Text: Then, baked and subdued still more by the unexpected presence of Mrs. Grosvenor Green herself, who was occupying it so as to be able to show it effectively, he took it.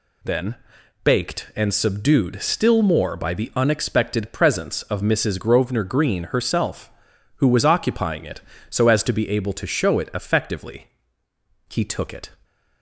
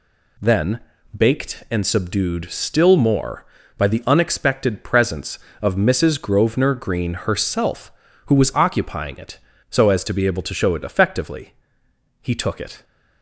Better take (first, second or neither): neither